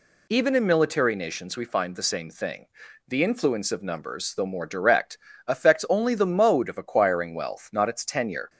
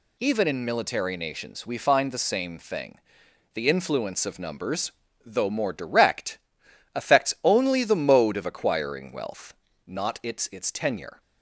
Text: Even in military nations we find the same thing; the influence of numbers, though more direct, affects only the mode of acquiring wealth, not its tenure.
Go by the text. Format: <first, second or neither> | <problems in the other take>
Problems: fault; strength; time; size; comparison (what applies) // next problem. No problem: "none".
first | says "its" twice; at 10.5 s